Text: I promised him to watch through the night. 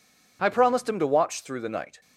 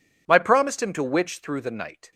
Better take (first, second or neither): first